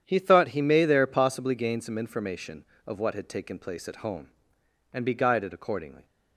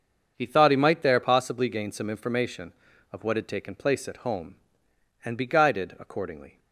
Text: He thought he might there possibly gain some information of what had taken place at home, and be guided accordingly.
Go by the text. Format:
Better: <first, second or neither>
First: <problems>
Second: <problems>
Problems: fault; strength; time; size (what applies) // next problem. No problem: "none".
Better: second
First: starts louder than the rest; strong; until 1.0 s; 9 dB // says "may" for "might"; at 0.6 s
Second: starts louder than the rest; until 1.3 s; 6.5 dB